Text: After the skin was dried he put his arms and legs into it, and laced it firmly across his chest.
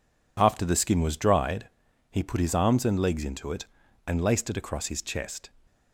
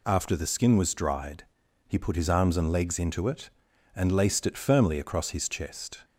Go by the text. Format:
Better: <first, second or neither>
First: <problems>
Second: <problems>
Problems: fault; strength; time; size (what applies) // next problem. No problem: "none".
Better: second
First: pauses between "dried" and "he"; at 1.6 s; 0.44 s long // skips "firmly"; at 4.5 s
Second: pauses between "dried" and "he"; at 1.4 s; 0.44 s long